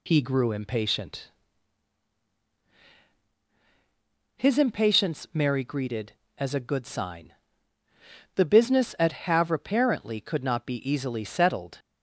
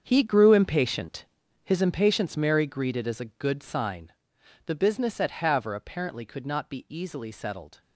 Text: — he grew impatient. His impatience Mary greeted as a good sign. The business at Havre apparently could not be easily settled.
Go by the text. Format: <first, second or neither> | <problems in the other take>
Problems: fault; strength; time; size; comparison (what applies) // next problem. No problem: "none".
first | gets quieter; strong; throughout; 13 dB